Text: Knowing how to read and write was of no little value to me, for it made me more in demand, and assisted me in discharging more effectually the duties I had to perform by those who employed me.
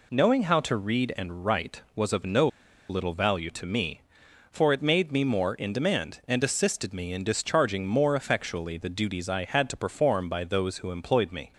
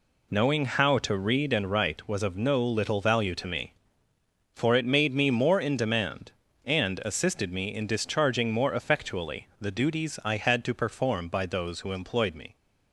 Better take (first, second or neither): second